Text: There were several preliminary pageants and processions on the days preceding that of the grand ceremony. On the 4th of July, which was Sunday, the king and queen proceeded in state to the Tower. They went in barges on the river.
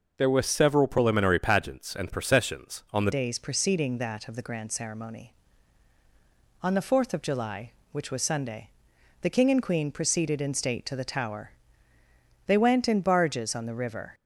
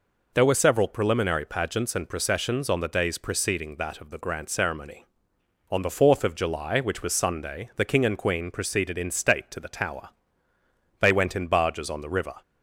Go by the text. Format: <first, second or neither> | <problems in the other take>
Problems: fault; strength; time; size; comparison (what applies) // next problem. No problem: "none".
second | changes voice at "days"; from 3.1 s on; 11.0 s long